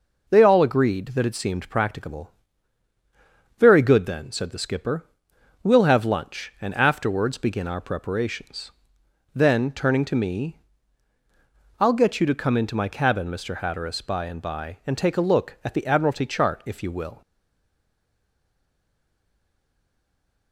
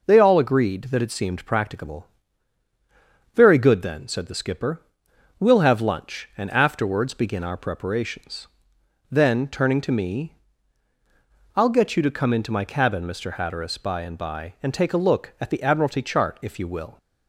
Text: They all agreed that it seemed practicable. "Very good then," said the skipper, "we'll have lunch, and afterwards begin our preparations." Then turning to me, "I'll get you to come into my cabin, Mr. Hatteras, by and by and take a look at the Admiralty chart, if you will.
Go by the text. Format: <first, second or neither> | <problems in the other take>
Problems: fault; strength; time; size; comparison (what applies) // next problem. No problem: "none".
second | stays silent after the last word; strong; from 17.2 s on; 3.3 s long